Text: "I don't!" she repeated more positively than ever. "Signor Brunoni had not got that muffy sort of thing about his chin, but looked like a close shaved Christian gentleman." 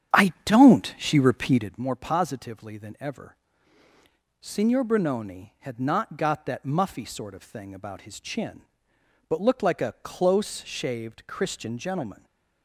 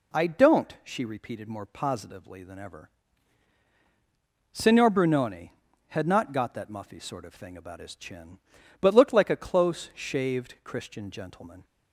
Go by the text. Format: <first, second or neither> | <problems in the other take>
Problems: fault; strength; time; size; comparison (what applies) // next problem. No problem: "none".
second | starts louder than the rest; strong; until 1.8 s; 9.5 dB